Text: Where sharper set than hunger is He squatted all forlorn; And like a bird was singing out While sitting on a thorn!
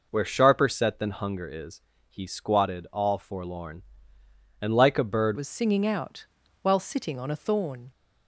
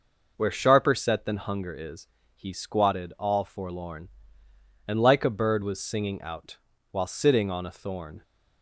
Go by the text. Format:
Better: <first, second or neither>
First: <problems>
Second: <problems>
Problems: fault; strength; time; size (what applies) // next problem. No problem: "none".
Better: second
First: pauses between "is" and "He"; slight; at 1.8 s; 0.28 s long // changes voice at "was"; from 5.3 s on; 2.5 s long // pauses between "out" and "While"; slight; at 6.2 s; 0.34 s long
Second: pauses between "is" and "He"; slight; at 2.0 s; 0.28 s long // pauses between "out" and "While"; slight; at 6.5 s; 0.34 s long